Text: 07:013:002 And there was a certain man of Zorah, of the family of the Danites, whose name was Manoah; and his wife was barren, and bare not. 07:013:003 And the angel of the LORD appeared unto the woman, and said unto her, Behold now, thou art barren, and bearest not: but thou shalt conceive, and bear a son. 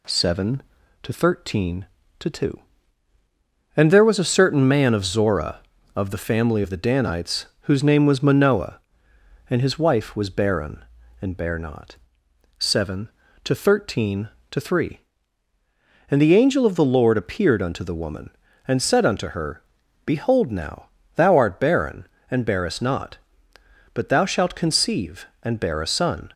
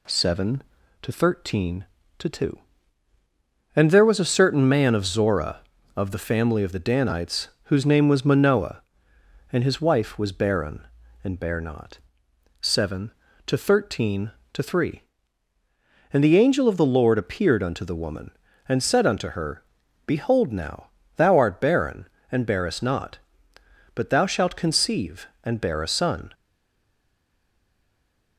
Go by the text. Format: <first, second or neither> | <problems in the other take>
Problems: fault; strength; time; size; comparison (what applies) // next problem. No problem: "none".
first | stays silent after the last word; noticeable; from 26.3 s on; 2.0 s long